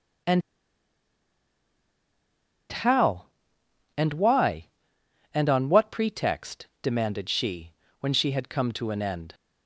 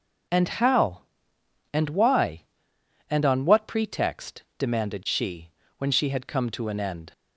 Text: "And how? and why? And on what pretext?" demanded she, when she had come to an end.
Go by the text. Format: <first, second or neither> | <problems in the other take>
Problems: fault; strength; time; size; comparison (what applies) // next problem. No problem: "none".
second | pauses between "And" and "how"; strong; at 0.4 s; 2.2 s long